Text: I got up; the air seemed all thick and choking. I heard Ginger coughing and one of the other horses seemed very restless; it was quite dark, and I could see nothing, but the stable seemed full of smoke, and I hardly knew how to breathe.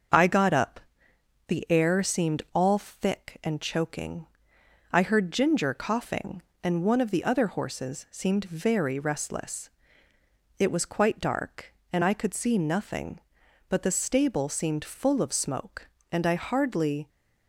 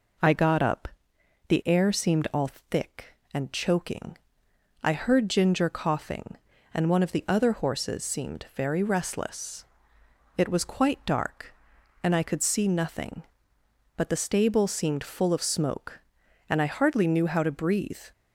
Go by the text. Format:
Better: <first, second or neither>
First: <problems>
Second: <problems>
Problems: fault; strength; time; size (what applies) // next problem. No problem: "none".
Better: second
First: starts louder than the rest; until 1.8 s; 7 dB // stops before "knew how to breathe"; at 17.0 s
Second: none